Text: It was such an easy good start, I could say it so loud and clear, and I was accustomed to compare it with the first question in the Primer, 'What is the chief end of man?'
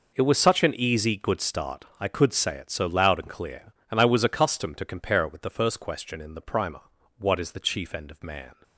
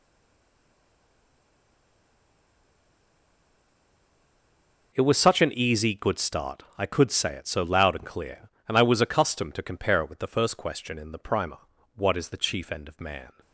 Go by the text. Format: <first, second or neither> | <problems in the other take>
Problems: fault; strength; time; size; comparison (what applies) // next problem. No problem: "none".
first | stays silent before the first word; strong; until 4.9 s; 4.9 s long